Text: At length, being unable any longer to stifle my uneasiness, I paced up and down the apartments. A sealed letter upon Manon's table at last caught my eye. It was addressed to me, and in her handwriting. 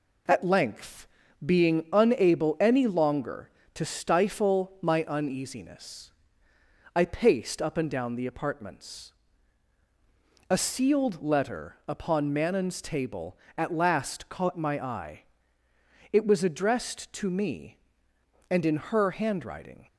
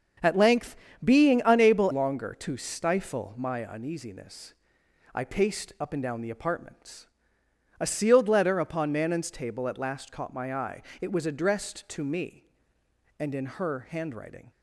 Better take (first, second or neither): first